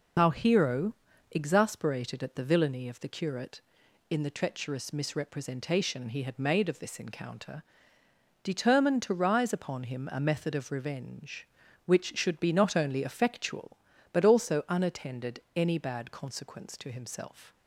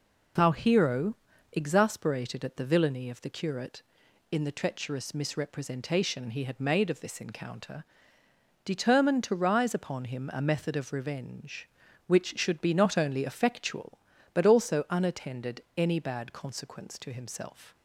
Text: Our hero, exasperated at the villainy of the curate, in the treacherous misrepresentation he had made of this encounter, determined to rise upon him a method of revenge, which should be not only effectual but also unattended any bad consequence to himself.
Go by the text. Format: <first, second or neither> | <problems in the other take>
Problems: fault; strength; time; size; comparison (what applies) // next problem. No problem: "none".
second | loses the start of "Our"; at 0.1 s; 30 ms // pauses between "unattended" and "any"; slight; at 15.4 s; 0.16 s long; slight in the second